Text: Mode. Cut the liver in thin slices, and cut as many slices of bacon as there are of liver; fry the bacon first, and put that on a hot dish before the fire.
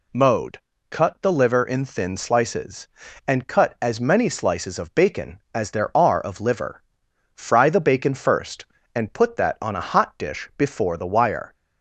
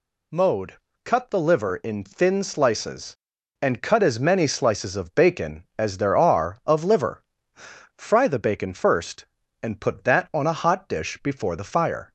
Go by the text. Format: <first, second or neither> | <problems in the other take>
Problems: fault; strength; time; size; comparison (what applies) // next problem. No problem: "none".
second | says "wire" for "fire"; at 11.0 s